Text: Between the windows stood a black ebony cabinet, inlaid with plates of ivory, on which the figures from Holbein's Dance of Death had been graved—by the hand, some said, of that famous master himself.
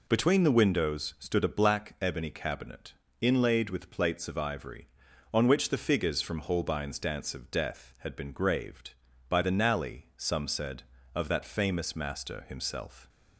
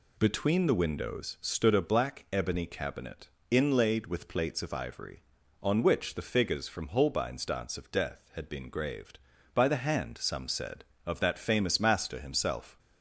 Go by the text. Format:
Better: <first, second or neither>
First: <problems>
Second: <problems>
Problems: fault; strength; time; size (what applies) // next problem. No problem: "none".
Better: second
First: says "nally" for "hand"; at 9.4 s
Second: none